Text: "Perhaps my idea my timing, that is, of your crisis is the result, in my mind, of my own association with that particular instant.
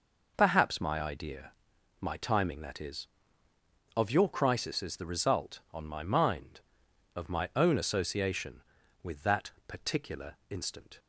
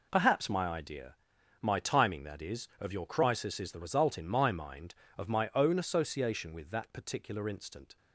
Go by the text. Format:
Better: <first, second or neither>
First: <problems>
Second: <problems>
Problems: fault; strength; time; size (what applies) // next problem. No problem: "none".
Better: second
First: pauses between "idea" and "my"; noticeable; at 1.5 s; 0.50 s long // says "on" for "in"; at 5.7 s // pauses between "that" and "particular"; slight; at 9.5 s; 0.16 s long // pauses between "particular" and "instant"; slight; at 10.3 s; 0.16 s long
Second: pauses between "idea" and "my"; noticeable; at 1.1 s; 0.46 s long